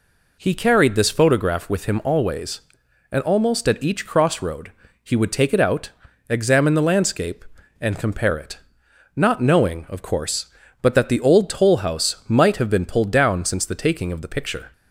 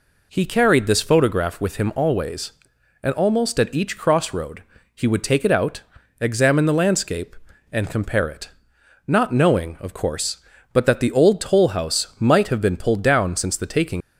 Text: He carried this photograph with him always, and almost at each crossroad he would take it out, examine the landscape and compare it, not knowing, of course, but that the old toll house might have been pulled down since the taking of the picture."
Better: first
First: pauses between "crossroad" and "he"; slight; at 4.7 s; 0.32 s long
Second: pauses between "crossroad" and "he"; slight; at 4.6 s; 0.32 s long // stops before "of the picture"; at 14.0 s

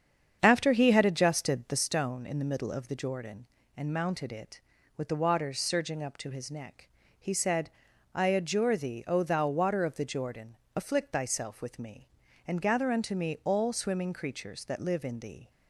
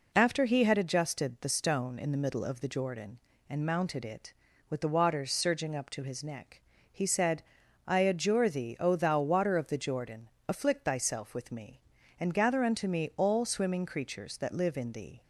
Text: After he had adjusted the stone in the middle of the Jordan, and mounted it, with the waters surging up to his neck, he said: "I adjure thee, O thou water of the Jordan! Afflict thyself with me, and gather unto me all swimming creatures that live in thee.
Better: second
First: starts louder than the rest; strong; until 2.0 s; 7.5 dB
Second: none

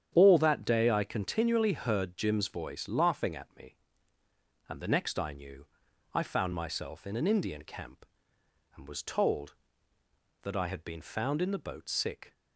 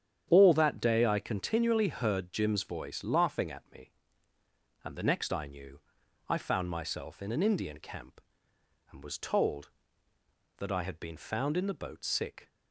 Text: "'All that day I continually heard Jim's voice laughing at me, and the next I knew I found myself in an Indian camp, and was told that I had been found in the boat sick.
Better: neither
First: starts louder than the rest; strong; until 1.1 s; 9 dB // pauses between "knew" and "I"; noticeable; at 5.6 s; 0.49 s long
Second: starts louder than the rest; strong; until 1.3 s; 9 dB // pauses between "knew" and "I"; noticeable; at 5.7 s; 0.50 s long

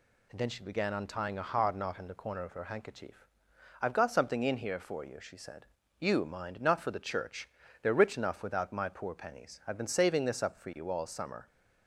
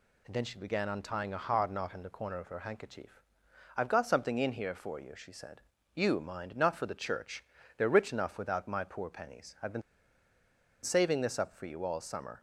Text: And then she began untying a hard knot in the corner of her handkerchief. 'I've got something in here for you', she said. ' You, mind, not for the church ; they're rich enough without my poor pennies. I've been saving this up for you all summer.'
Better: first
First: none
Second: pauses between "been" and "saving"; at 9.8 s; 1.0 s long

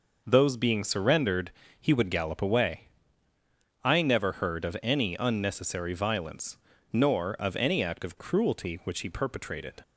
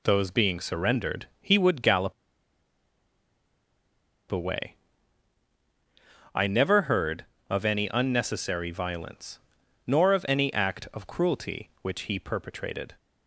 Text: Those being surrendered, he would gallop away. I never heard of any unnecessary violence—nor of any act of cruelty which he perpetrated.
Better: first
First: none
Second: pauses between "gallop" and "away"; strong; at 2.1 s; 2.1 s long

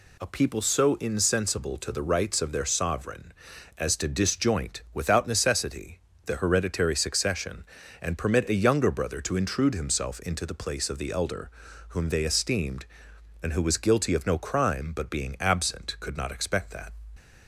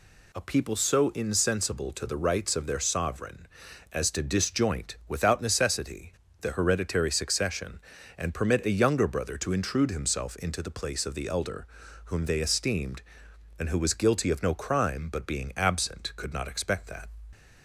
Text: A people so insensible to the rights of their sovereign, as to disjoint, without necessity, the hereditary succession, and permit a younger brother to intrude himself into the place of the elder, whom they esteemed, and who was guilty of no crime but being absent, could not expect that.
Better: neither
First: none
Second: none

